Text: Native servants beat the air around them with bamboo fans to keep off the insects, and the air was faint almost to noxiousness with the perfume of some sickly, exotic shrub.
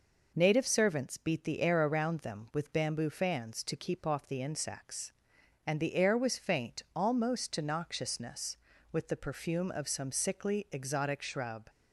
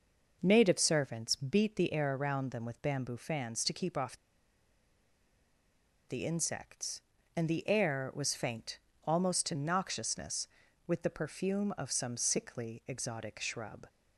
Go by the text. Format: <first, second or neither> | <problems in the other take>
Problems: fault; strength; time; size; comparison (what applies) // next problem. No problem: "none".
first | pauses between "off" and "the"; strong; at 4.1 s; 1.9 s long // pauses between "faint" and "almost"; slight; at 8.7 s; 0.24 s long